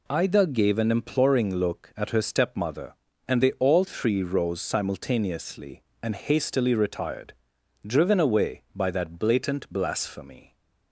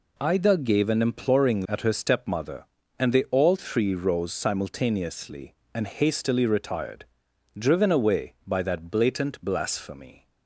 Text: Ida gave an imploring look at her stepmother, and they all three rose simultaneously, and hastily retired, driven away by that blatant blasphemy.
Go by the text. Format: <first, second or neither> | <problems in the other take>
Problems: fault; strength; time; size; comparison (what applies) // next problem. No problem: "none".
first | skips "look"; at 1.6 s